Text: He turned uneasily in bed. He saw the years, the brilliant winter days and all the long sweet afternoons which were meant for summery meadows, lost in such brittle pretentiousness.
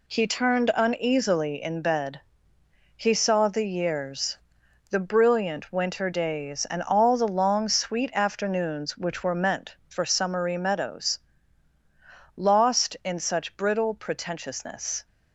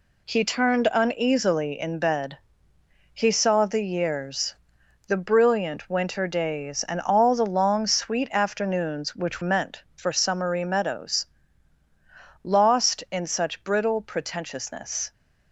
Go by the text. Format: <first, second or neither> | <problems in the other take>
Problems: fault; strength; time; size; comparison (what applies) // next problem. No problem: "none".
first | skips "were"; at 9.4 s